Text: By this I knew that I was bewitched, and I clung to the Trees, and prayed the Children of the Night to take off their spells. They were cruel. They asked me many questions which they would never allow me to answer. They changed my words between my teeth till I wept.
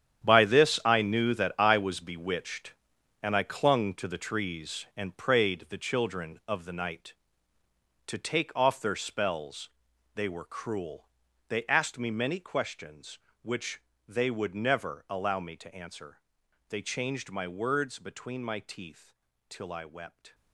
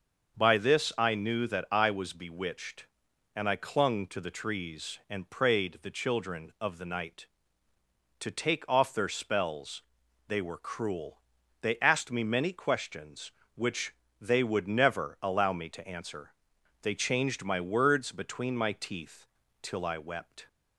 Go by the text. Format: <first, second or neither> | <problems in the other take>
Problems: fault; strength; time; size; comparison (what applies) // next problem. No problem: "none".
second | gets quieter; strong; throughout; 13.5 dB // starts louder than the rest; strong; until 1.3 s; 9 dB; also in the second // pauses between "which" and "they"; slight; at 13.8 s; 0.26 s long; slight in the second // pauses between "teeth" and "till"; slight; at 19.1 s; 0.34 s long; slight in the second